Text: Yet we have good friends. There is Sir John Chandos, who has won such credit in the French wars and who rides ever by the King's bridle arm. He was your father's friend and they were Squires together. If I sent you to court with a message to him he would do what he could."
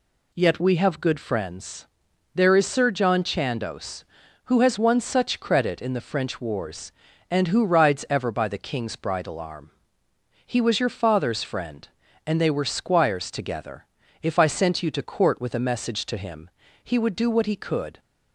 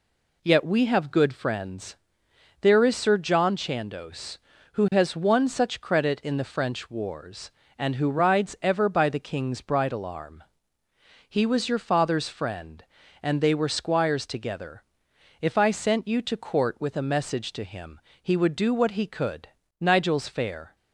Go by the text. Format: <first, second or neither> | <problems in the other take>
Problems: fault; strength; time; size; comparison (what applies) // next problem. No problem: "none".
first | pauses between "him" and "he"; slight; at 17.9 s; 0.22 s long; slight in the first // goes on to say "Nigel's fair"; noticeable; from 19.7 s on; 0.96 s long